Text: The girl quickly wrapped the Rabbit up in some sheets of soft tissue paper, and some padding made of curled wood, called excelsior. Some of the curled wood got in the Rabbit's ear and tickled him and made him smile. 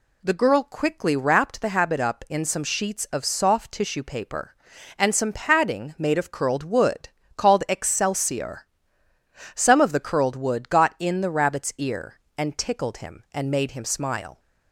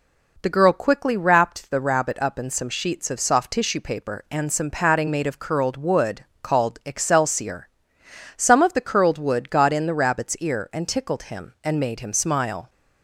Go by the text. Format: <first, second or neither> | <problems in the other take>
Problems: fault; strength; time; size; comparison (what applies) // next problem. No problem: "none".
second | says "Habit" for "Rabbit"; at 1.6 s